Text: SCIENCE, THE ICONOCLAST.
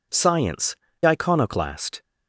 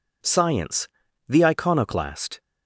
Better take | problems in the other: second | skips "THE"; at 0.9 s

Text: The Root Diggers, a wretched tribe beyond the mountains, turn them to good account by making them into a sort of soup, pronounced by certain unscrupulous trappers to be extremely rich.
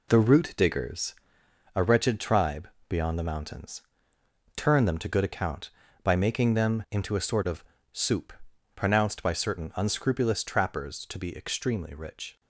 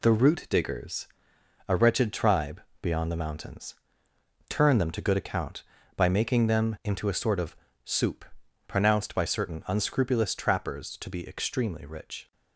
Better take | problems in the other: second | starts louder than the rest; slight; until 1.5 s; 2.5 dB // pauses between "tribe" and "beyond"; slight; at 2.6 s; 0.22 s long; slight in the second // pauses between "of" and "soup"; slight; at 7.6 s; 0.30 s long; slight in the second

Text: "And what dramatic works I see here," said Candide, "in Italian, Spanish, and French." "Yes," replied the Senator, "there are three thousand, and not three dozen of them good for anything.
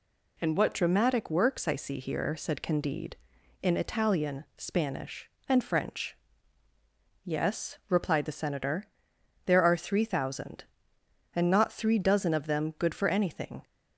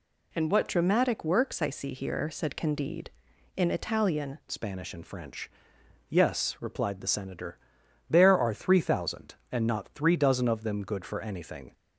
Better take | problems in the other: first | changes voice at "Spanish"; from 4.4 s on; 7.3 s long

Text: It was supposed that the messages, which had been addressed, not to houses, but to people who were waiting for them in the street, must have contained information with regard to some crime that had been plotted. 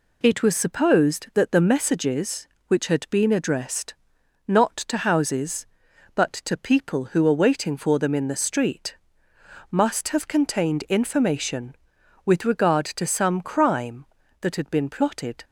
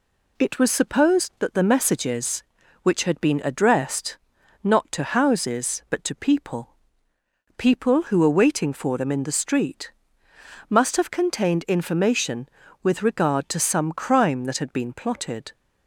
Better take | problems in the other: first | says "people" twice; at 7.5 s

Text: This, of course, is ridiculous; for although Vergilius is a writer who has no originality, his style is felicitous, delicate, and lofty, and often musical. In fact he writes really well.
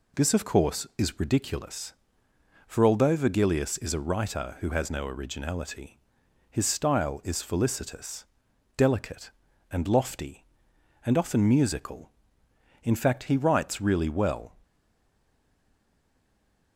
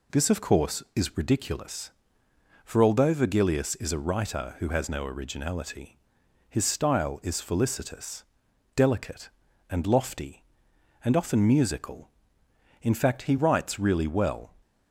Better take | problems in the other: second | stays silent after the last word; from 14.6 s on; 2.1 s long

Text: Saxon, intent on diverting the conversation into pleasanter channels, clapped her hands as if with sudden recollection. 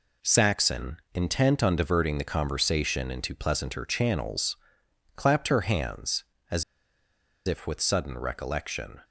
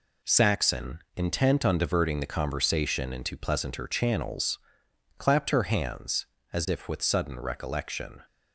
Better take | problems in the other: second | pauses between "as" and "if"; noticeable; at 6.6 s; 0.83 s long

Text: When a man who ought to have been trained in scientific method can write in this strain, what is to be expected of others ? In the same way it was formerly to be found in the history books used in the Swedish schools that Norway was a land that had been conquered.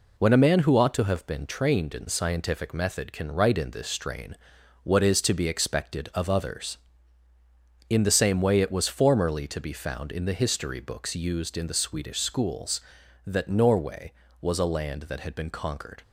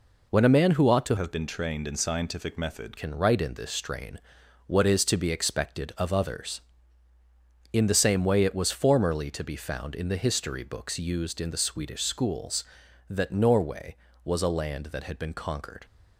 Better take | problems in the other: first | changes voice from "have" to "method"; from 1.1 to 2.9 s; 1.8 s long

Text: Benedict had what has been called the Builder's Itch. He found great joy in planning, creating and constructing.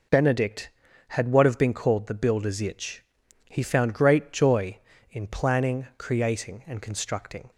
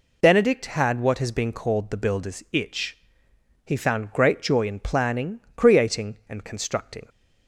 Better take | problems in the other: second | says "have" for "has"; at 1.4 s

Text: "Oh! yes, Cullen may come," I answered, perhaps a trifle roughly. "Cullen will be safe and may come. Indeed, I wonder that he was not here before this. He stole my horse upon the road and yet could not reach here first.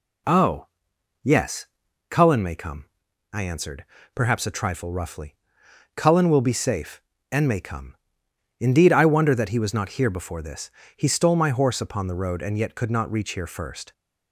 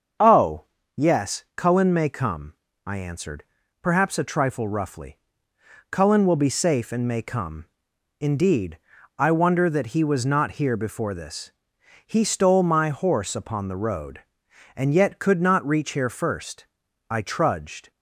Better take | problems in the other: first | starts louder than the rest; until 1.6 s; 6.5 dB // goes on to say "I trudged"; noticeable; from 17.1 s on; 0.80 s long

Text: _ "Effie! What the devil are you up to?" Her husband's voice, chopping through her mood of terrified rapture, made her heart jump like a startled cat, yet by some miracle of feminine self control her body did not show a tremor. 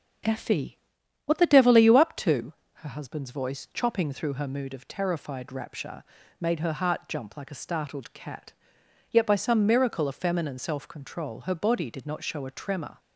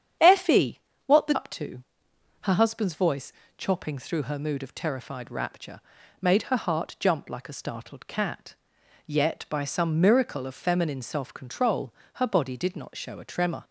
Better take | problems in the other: first | starts louder than the rest; strong; until 1.4 s; 8.5 dB; also in the first // skips "devil are you"; at 1.3 s // pauses between "control" and "her"; slight; at 11.9 s; 0.22 s long

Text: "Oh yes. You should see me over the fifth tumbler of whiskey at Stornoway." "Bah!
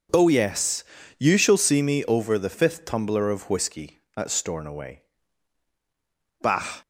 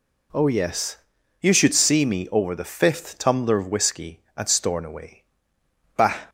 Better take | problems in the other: second | says "shall" for "should"; at 1.3 s

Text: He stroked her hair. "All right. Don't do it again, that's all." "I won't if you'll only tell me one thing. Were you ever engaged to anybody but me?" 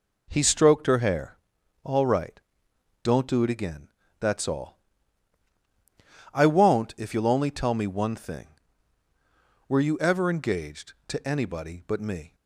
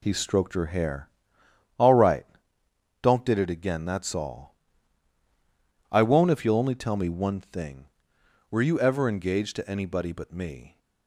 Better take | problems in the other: first | says "did" for "do"; at 3.2 s

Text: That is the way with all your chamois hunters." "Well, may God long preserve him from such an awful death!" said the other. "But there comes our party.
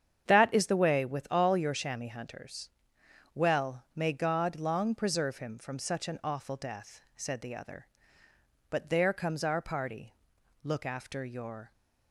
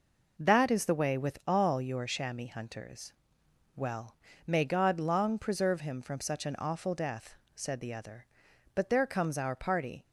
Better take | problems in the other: second | starts louder than the rest; strong; until 1.3 s; 8.5 dB // goes on to say "Look after your"; noticeable; from 10.6 s on; 1.0 s long

